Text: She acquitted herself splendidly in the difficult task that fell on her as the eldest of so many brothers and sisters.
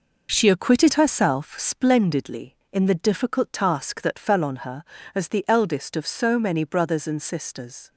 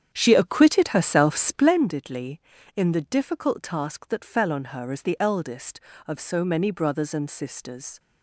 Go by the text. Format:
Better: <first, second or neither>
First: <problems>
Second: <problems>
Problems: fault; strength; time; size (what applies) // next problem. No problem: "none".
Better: first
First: none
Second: starts louder than the rest; strong; until 1.9 s; 8 dB